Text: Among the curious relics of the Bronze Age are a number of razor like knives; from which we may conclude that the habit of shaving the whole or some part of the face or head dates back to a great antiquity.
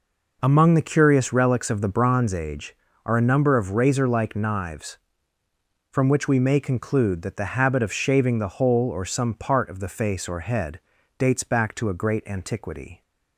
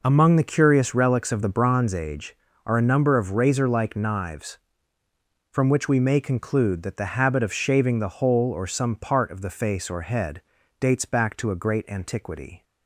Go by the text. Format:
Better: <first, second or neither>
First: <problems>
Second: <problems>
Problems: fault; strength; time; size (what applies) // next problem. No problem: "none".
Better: neither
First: pauses between "head" and "dates"; at 10.7 s; 0.40 s long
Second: pauses between "head" and "dates"; at 10.3 s; 0.40 s long